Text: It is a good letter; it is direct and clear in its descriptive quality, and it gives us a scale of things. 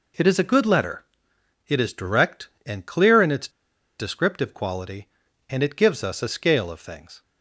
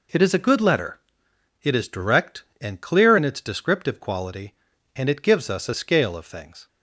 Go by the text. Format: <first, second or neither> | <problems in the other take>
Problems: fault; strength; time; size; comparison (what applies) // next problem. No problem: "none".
second | pauses between "its" and "descriptive"; noticeable; at 3.4 s; 0.49 s long